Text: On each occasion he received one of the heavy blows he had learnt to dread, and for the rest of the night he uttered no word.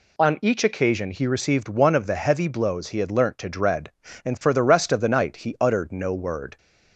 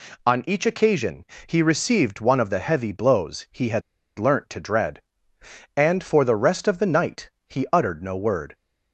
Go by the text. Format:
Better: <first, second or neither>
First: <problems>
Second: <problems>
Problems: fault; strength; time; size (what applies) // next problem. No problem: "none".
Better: first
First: none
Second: pauses between "occasion" and "he"; slight; at 1.2 s; 0.20 s long // pauses between "had" and "learnt"; at 3.8 s; 0.36 s long // pauses between "night" and "he"; slight; at 7.3 s; 0.18 s long